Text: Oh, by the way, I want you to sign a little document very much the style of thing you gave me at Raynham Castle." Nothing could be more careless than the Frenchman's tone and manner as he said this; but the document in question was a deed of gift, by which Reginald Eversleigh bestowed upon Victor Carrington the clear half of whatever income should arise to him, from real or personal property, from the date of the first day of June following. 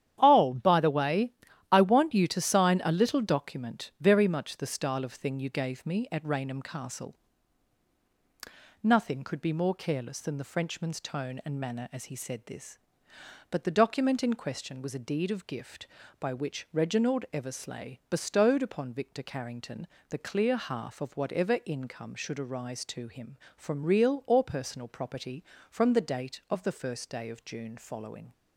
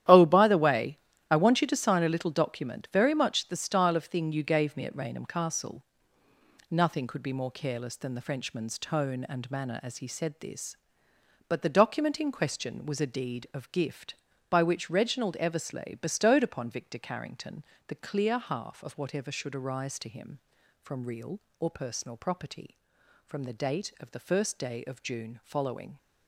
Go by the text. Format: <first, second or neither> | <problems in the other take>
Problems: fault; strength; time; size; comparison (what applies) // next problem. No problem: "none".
first | starts louder than the rest; strong; until 1.3 s; 11.5 dB; strong in the first // pauses between "Carrington" and "the"; slight; at 17.6 s; 0.22 s long; slight in the first // skips "income"; at 19.3 s